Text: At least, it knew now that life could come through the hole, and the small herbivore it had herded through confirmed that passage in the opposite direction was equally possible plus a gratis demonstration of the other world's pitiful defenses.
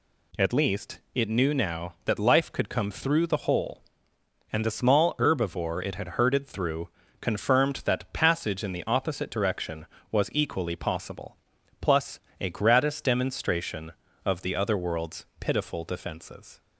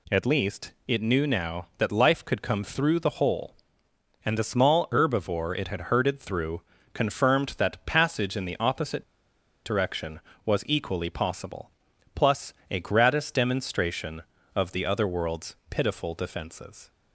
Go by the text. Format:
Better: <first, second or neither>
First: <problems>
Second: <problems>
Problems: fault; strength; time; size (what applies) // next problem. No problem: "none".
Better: first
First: pauses between "through" and "confirmed"; slight; at 6.8 s; 0.30 s long // pauses between "possible" and "plus"; at 11.3 s; 0.44 s long // pauses between "plus" and "a"; slight; at 12.1 s; 0.21 s long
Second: pauses between "through" and "confirmed"; slight; at 6.6 s; 0.30 s long // pauses between "opposite" and "direction"; noticeable; at 9.0 s; 0.61 s long // pauses between "possible" and "plus"; at 11.7 s; 0.44 s long // pauses between "plus" and "a"; slight; at 12.5 s; 0.18 s long